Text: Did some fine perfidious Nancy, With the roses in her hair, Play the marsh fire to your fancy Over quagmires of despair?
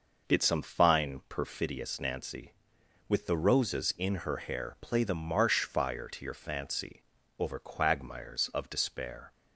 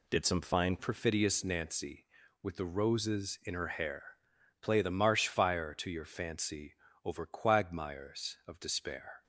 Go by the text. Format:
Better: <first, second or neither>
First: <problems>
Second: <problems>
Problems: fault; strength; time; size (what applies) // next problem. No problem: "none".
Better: first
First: pauses between "fancy" and "Over"; slight; at 7.0 s; 0.36 s long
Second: changes voice at "perfidious"; from 0.7 s on; 8.5 s long // pauses between "fancy" and "Over"; slight; at 6.7 s; 0.28 s long